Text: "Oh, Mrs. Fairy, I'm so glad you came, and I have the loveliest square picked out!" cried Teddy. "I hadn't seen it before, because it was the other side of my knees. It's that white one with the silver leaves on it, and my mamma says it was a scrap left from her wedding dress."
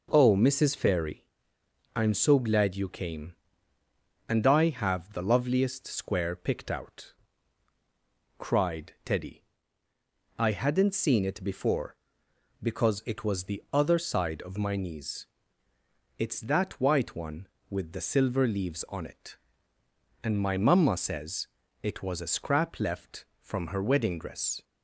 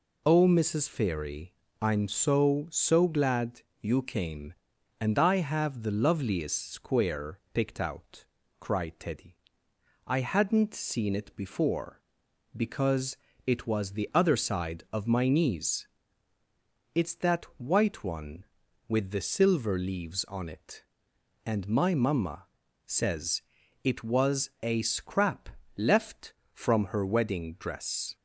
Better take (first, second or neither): first